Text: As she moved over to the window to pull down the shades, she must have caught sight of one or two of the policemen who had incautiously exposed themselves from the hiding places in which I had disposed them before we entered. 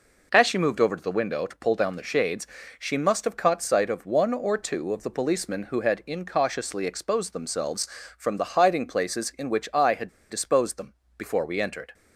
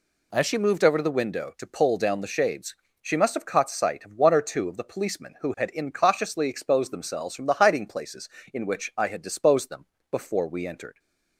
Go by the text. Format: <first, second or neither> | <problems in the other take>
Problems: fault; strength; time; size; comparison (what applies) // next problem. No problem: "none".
second | pauses between "had" and "disposed"; slight; at 10.0 s; 0.20 s long // pauses between "them" and "before"; slight; at 10.9 s; 0.24 s long; slight in the second